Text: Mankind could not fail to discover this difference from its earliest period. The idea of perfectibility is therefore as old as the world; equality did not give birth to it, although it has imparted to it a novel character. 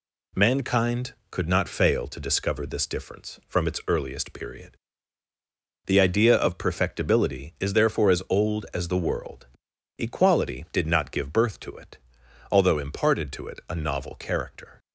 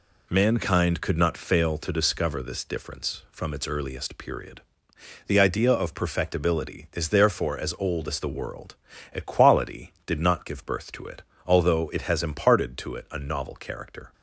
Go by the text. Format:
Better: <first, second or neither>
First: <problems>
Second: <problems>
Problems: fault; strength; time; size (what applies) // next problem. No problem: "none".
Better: second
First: skips "it has"; at 12.7 s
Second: none